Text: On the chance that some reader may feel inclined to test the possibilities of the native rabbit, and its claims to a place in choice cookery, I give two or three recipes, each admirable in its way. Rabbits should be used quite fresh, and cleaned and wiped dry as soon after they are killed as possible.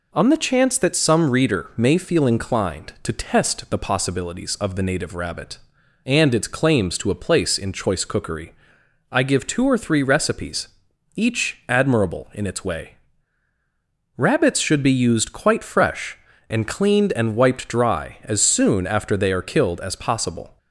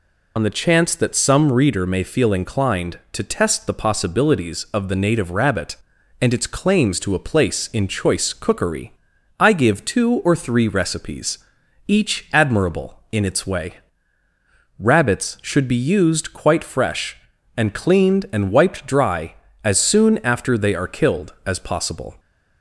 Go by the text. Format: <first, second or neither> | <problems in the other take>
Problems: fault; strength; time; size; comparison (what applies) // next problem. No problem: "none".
first | loses the start of "On"; at 0.3 s; 65 ms